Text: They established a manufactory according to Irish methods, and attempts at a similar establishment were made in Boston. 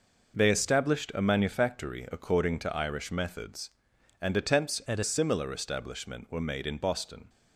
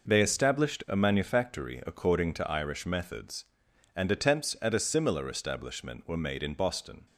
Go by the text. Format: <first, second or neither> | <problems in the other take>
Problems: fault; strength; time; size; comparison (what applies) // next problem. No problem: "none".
second | changes voice from "at" to "a"; from 4.8 to 5.0 s; 0.2 s long